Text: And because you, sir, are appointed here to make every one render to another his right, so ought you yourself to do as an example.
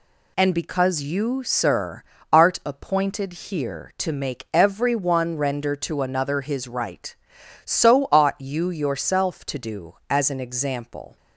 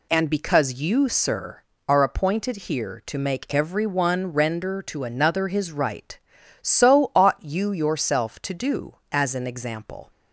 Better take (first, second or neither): second